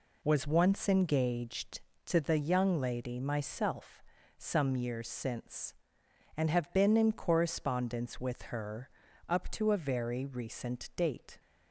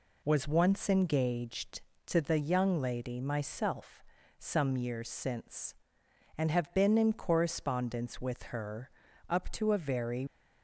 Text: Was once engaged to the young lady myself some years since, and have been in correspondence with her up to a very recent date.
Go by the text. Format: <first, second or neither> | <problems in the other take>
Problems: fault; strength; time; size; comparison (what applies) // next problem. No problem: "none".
first | pauses between "myself" and "some"; slight; at 4.0 s; 0.34 s long; slight in the first // pauses between "her" and "up"; at 8.8 s; 0.40 s long; also in the first // stops before "recent date"; at 10.2 s